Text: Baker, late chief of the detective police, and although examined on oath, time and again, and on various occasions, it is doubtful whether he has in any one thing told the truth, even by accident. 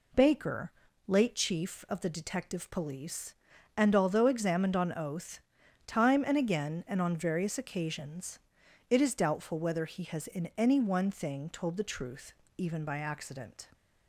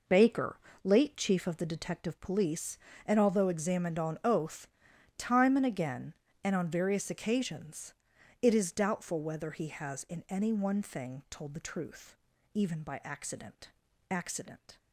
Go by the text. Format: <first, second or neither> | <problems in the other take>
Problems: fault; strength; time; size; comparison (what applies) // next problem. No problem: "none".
first | says "accident" twice; at 14.0 s